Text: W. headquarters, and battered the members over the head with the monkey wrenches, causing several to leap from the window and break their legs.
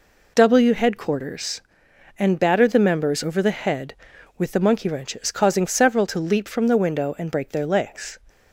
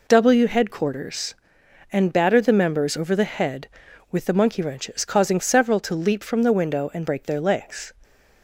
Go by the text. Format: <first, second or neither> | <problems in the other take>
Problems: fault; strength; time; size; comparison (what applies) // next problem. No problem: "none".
neither | none